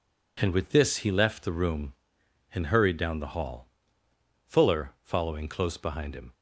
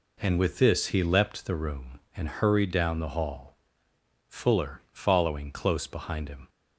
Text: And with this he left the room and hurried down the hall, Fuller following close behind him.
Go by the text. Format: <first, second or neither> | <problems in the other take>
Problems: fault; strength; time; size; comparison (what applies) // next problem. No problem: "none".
first | says "leapt" for "left"; at 1.0 s